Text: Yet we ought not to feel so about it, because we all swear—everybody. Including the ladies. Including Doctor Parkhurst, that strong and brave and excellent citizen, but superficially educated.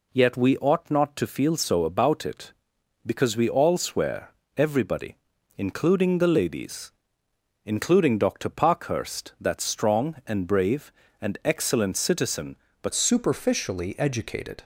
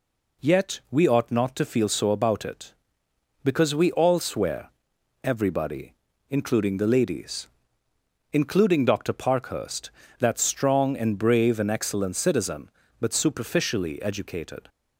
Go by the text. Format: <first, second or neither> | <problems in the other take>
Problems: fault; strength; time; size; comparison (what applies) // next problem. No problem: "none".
second | changes voice at "superficially"; from 12.9 s on; 1.7 s long